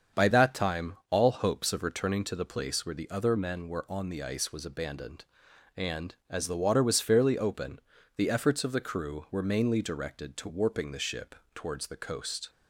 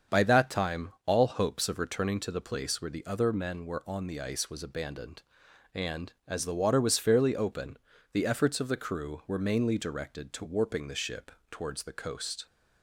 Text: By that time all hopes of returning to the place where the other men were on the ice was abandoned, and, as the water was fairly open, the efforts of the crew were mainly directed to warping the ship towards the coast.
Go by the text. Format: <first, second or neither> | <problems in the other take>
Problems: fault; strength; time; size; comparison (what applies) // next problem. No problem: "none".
neither | starts louder than the rest; strong; the same in both // pauses between "ship" and "towards"; slight; the same in both